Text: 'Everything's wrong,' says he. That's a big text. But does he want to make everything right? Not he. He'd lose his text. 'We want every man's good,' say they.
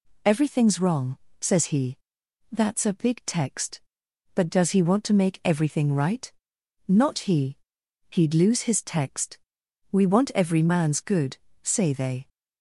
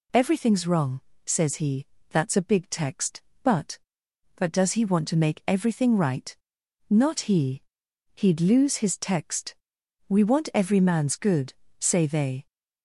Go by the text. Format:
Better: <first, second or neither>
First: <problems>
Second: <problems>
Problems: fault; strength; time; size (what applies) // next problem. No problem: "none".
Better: first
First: none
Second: says "But" twice; at 4.3 s